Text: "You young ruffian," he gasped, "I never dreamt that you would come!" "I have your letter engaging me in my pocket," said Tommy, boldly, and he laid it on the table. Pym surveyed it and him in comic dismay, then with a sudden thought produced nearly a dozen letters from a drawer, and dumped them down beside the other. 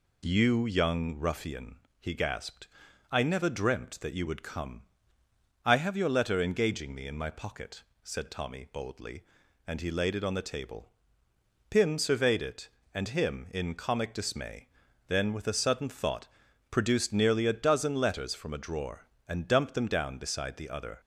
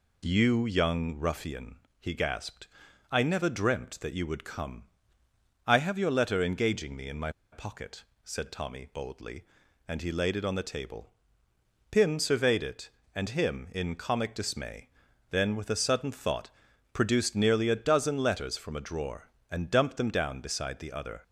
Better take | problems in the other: first | pauses between "my" and "pocket"; slight; at 7.2 s; 0.22 s long // pauses between "thought" and "produced"; at 16.5 s; 0.42 s long; also in the first

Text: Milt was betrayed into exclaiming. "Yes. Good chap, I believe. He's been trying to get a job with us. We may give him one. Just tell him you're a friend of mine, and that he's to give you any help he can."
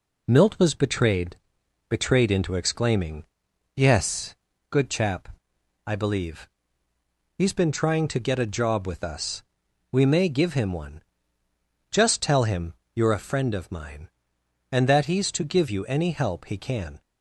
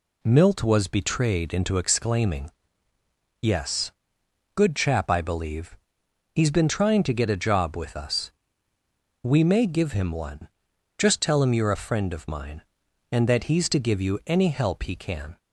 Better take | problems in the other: second | says "betrayed" twice; at 1.9 s // pauses between "him" and "you're"; slight; at 12.7 s; 0.22 s long

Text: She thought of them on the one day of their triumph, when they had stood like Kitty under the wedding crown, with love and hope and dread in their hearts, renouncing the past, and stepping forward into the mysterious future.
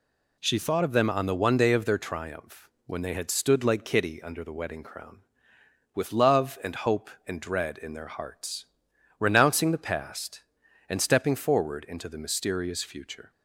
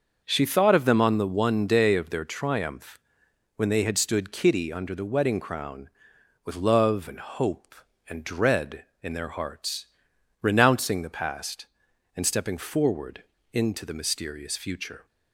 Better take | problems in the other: first | starts louder than the rest; until 1.2 s; 6 dB // skips "like"; at 4.3 s // pauses between "forward" and "into"; slight; at 13.2 s; 0.28 s long

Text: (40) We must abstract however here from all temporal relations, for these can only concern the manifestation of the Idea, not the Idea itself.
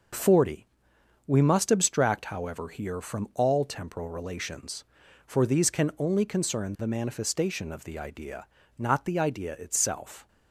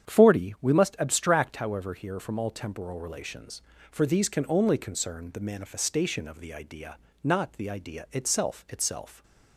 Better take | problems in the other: first | starts louder than the rest; strong; until 1.1 s; 8.5 dB // says "itself" twice; at 8.6 s

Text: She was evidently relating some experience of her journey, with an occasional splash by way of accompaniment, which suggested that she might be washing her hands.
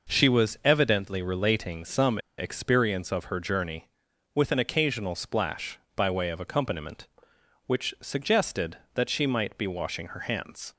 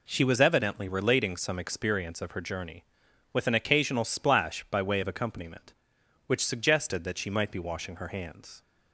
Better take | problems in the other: second | pauses between "some" and "experience"; slight; at 2.1 s; 0.20 s long

